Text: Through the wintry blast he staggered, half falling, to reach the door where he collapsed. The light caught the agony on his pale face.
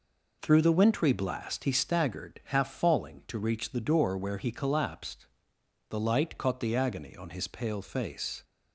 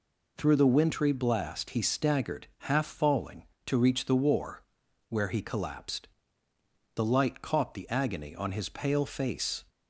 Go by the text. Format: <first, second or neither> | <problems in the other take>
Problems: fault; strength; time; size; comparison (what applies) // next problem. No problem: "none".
first | says "war" for "door"; at 4.1 s